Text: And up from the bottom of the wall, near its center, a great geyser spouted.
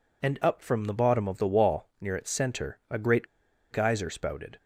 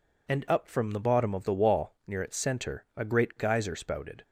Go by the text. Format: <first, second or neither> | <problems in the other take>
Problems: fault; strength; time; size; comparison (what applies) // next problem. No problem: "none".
second | pauses between "great" and "geyser"; at 3.2 s; 0.45 s long